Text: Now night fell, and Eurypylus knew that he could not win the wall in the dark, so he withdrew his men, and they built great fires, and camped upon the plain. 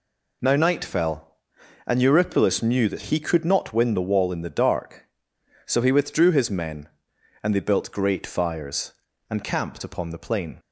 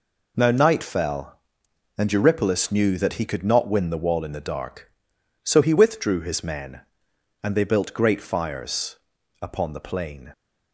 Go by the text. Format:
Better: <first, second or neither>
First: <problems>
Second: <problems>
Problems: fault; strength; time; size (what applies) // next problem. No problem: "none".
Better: first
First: none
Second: skips "and camped"; at 9.1 s